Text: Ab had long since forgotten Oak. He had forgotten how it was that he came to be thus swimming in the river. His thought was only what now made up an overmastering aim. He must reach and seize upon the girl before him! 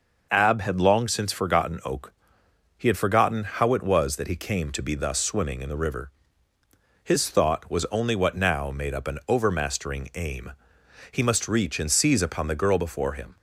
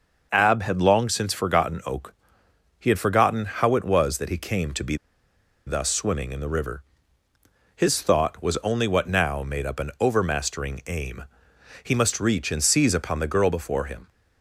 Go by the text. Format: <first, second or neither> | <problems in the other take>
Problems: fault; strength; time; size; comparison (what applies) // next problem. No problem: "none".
first | pauses between "be" and "thus"; noticeable; at 4.9 s; 0.71 s long